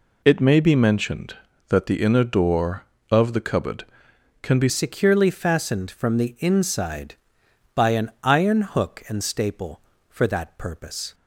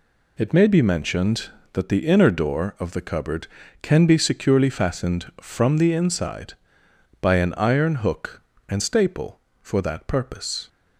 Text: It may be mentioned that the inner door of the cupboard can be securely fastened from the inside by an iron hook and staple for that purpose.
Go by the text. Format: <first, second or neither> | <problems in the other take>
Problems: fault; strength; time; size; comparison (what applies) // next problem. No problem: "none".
second | changes voice at "securely"; from 4.6 s on; 6.5 s long